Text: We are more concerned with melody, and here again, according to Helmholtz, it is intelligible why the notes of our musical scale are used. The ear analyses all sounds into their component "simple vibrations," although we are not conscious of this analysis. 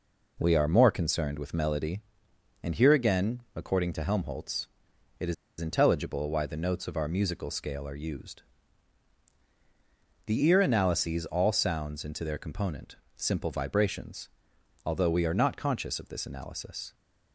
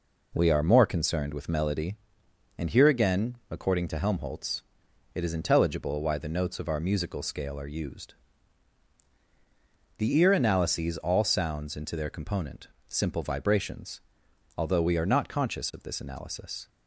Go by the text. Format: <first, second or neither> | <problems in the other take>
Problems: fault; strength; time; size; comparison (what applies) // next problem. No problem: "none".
second | pauses between "is" and "intelligible"; slight; at 5.3 s; 0.24 s long // pauses between "component" and "simple"; slight; at 12.9 s; 0.22 s long; slight in the second